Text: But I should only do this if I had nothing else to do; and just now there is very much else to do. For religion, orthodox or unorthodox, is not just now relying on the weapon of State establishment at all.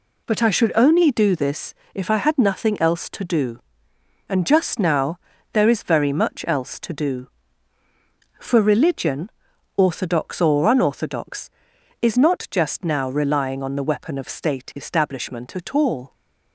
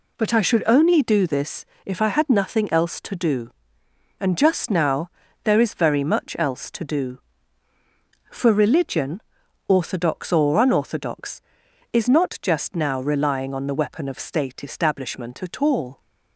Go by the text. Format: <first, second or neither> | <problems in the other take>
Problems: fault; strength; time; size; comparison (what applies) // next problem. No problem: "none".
neither | pauses between "this" and "if"; slight; the same in both // pauses between "now" and "there"; slight; the same in both